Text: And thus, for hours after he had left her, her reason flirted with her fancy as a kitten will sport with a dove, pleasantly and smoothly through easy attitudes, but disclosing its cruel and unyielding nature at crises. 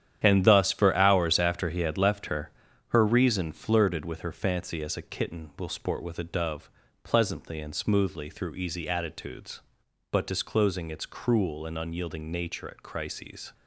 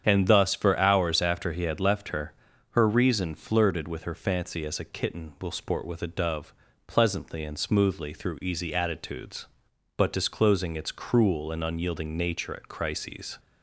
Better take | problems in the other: second | gets quieter; strong; throughout; 9.5 dB // starts louder than the rest; strong; until 1.2 s; 10 dB; strong in the second

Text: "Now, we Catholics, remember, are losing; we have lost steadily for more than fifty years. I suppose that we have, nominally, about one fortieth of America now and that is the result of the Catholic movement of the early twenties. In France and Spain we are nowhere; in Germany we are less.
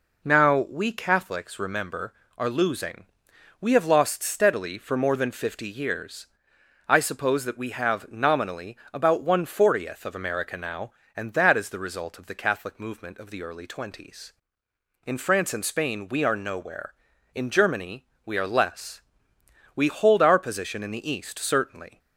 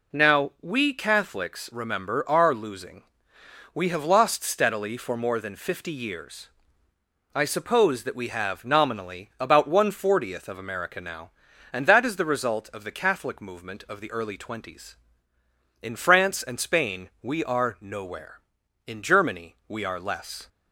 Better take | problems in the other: second | pauses between "Germany" and "we"; slight; at 18.0 s; 0.18 s long // goes on to say "We hold our position in the East certainly"; strong; from 19.7 s on; 2.2 s long

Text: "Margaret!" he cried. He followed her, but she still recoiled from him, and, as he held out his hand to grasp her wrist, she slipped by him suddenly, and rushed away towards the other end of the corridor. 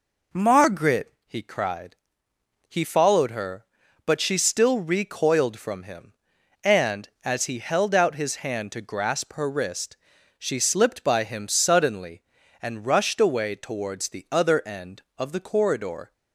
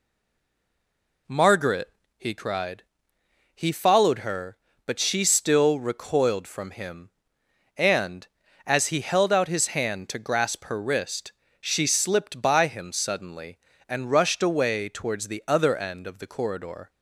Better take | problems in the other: first | stays silent before the first word; noticeable; until 1.2 s; 1.2 s long

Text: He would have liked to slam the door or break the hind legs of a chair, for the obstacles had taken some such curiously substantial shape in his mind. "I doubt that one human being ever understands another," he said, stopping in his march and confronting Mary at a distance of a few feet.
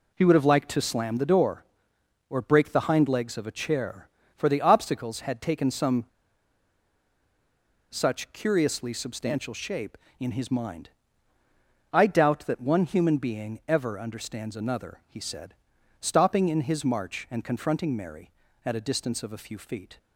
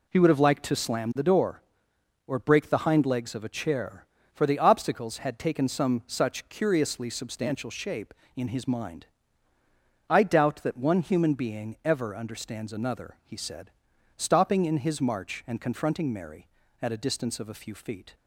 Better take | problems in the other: second | pauses between "some" and "such"; strong; at 6.0 s; 1.8 s long

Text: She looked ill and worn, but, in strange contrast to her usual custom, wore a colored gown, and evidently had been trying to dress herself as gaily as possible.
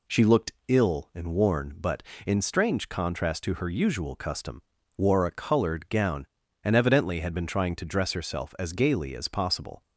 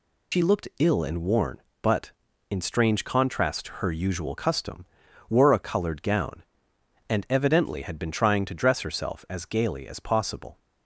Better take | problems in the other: first | loses the start of "She"; at 0.3 s; 90 ms

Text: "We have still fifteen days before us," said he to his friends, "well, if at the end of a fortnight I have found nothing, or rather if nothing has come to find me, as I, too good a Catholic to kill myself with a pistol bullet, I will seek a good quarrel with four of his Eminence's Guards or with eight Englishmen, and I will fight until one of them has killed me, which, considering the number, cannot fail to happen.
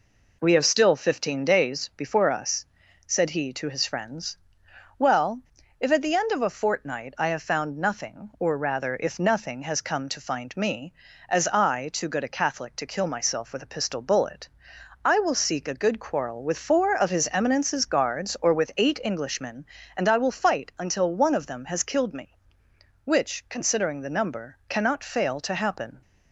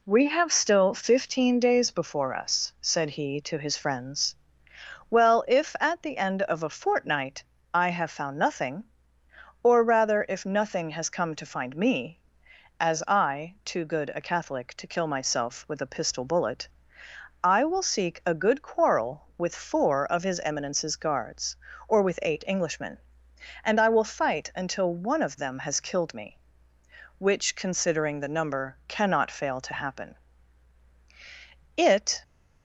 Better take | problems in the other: first | pauses between "fortnight" and "I"; slight; at 7.4 s; 0.30 s long // goes on to say "It"; slight; from 31.7 s on; 0.44 s long

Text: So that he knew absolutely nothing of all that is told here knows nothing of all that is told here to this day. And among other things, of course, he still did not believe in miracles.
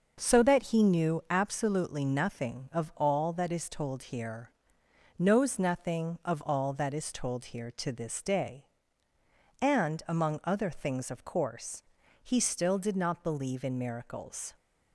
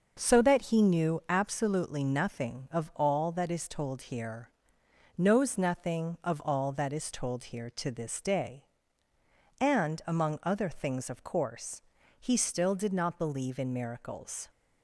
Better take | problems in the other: neither | starts louder than the rest; noticeable; the same in both // pauses between "here" and "knows"; noticeable; the same in both

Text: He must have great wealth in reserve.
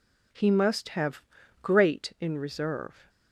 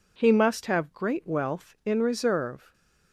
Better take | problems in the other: second | pauses between "have" and "great"; at 1.2 s; 0.40 s long // skips "wealth"; at 2.1 s

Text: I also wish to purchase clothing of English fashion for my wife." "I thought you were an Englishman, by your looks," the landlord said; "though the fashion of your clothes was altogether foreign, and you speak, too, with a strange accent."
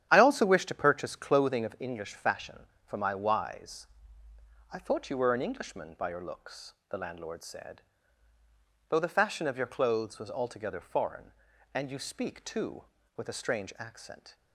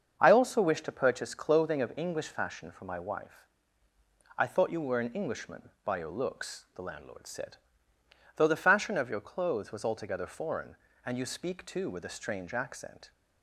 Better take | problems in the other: second | starts louder than the rest; strong; until 1.1 s; 10 dB; also in the second // says "wise" for "wife"; at 3.1 s

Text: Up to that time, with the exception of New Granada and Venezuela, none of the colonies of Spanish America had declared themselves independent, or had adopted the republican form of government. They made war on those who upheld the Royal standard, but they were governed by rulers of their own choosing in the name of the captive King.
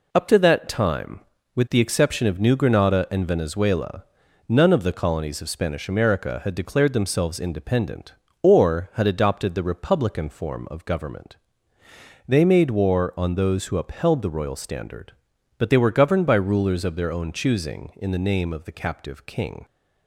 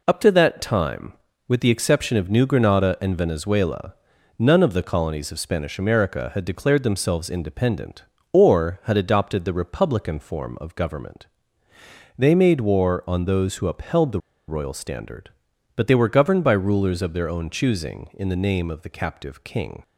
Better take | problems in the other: first | pauses between "the" and "Royal"; slight; at 14.1 s; 0.29 s long

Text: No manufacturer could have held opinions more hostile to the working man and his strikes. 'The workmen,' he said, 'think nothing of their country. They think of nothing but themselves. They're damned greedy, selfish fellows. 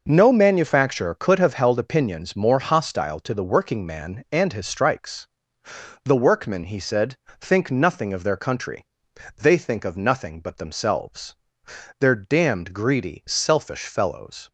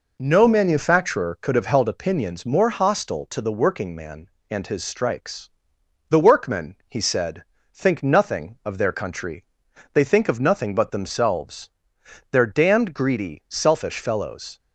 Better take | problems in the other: neither | none

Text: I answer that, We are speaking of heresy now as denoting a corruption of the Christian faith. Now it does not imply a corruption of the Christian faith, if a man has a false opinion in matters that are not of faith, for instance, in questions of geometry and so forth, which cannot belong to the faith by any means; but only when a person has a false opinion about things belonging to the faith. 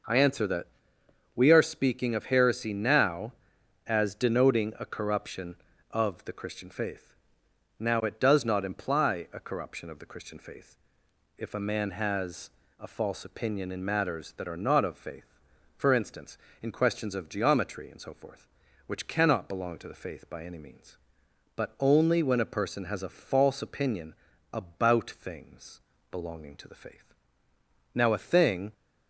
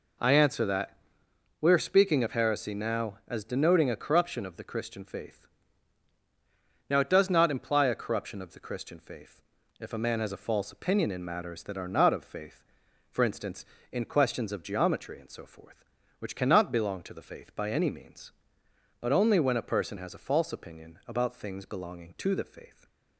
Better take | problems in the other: second | pauses between "has" and "a"; slight; at 12.5 s; 0.28 s long // pauses between "opinion" and "about"; at 24.1 s; 0.38 s long // pauses between "things" and "belonging"; slight; at 25.8 s; 0.30 s long // goes on to say "Now a thing"; noticeable; from 27.9 s on; 0.80 s long

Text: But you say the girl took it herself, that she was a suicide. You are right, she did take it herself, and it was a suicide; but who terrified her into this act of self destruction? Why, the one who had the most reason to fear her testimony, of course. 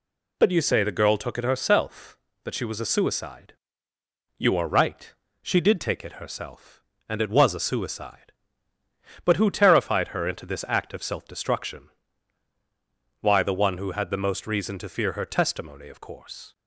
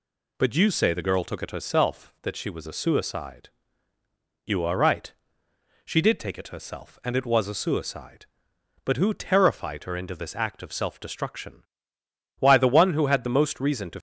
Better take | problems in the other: first | stops before "fear her testimony of course"; at 13.9 s

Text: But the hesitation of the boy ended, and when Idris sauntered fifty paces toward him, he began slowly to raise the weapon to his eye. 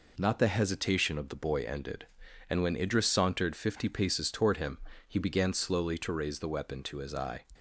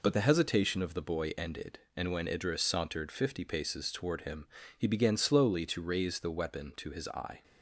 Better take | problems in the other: second | says "Not" for "But"; at 0.1 s

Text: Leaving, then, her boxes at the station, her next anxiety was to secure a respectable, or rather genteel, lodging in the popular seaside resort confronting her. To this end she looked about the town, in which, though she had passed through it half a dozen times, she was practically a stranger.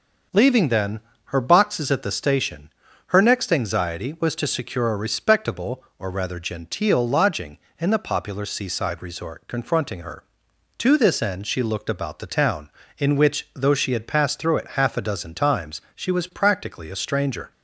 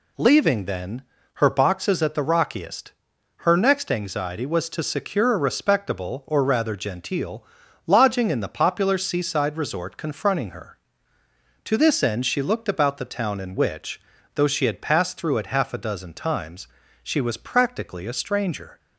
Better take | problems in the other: first | says "rockiest" for "station"; at 2.2 s

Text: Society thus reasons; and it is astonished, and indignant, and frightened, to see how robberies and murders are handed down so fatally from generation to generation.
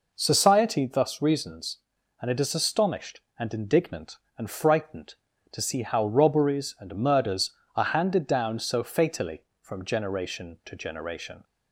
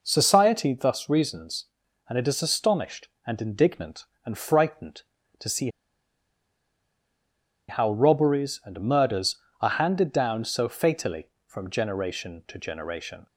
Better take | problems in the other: first | pauses between "see" and "how"; strong; at 5.6 s; 2.0 s long

